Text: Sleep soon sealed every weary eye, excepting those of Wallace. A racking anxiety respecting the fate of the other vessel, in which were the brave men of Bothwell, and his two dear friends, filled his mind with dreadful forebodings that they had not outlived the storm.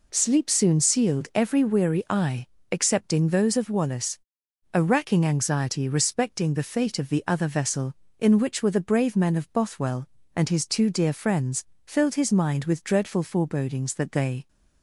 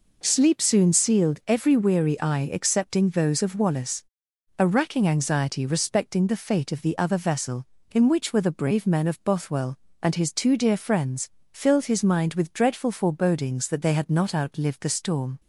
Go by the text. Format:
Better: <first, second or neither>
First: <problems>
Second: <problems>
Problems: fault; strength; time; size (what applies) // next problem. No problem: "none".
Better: second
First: stops before "had not outlived the storm"; at 14.4 s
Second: none